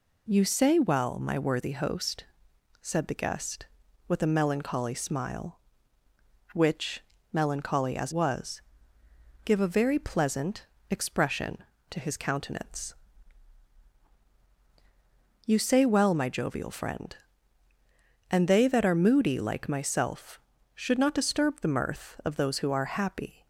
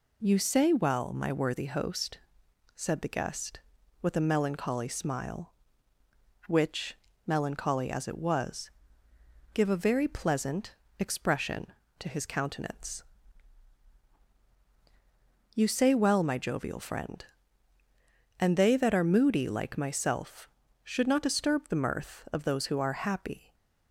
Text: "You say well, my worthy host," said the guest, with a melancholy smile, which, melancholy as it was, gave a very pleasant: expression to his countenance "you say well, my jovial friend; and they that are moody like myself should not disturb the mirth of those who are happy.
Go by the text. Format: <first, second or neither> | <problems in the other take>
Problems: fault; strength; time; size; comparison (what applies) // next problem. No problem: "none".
second | skips "it"; at 8.1 s // pauses between "countenance" and "you"; strong; at 12.9 s; 2.5 s long; strong in the second